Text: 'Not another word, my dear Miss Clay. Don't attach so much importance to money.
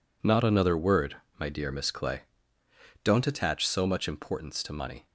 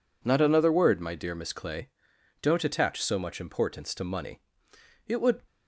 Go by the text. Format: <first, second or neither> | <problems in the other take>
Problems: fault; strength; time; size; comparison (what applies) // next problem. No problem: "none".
first | goes on to say "It would"; slight; from 5.0 s on; 0.34 s long